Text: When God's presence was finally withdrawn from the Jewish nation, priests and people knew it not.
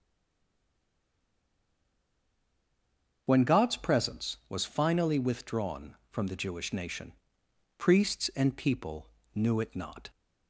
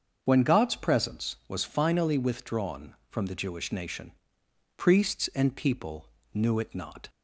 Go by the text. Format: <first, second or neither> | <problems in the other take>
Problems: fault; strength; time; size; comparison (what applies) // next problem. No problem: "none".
second | stays silent before the first word; strong; until 3.2 s; 3.2 s long // starts louder than the rest; until 4.2 s; 6.5 dB; also in the second // pauses between "people" and "knew"; slight; at 9.0 s; 0.26 s long; slight in the second